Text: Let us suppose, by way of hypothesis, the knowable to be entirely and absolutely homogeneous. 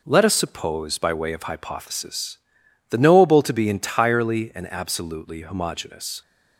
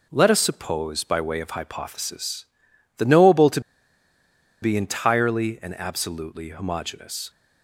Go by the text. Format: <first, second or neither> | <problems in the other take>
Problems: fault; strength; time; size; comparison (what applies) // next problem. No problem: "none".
first | pauses between "to" and "be"; at 3.6 s; 1.0 s long